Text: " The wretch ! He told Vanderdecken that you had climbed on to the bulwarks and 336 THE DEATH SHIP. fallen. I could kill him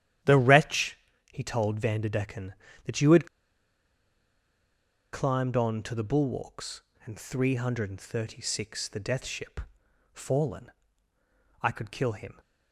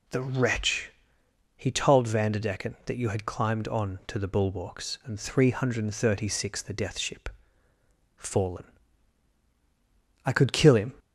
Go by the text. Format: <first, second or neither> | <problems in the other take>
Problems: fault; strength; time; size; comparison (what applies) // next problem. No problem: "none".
second | starts louder than the rest; strong; until 1.5 s; 11 dB // pauses between "had" and "climbed"; strong; at 3.2 s; 1.8 s long